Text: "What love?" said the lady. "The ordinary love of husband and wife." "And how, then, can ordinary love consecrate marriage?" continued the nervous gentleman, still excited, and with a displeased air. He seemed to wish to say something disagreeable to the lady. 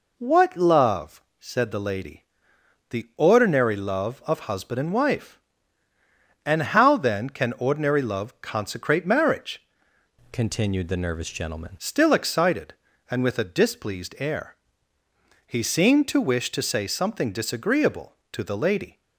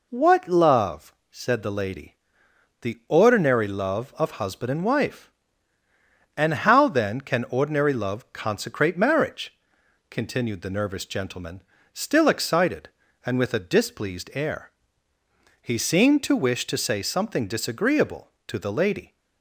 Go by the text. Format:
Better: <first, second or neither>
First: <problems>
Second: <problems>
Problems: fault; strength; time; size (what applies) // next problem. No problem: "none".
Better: second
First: changes voice from "continued" to "gentleman"; from 10.3 to 11.7 s; 1.4 s long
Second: none